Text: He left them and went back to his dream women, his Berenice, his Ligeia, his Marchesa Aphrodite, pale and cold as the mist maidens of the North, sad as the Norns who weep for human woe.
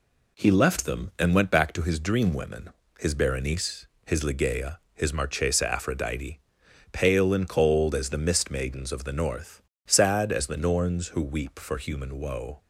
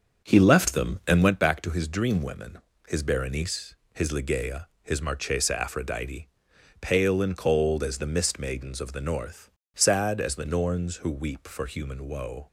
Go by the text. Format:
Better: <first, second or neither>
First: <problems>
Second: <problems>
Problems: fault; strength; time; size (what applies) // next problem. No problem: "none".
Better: first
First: none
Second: starts louder than the rest; until 1.4 s; 7 dB